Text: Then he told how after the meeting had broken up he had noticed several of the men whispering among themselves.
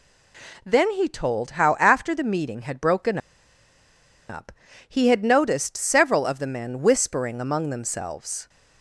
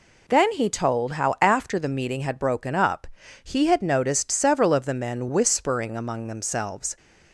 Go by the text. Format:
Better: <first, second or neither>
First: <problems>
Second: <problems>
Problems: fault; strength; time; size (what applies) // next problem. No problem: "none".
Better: second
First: pauses between "broken" and "up"; at 3.1 s; 1.1 s long // pauses between "up" and "he"; at 4.5 s; 0.38 s long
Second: pauses between "up" and "he"; slight; at 3.0 s; 0.36 s long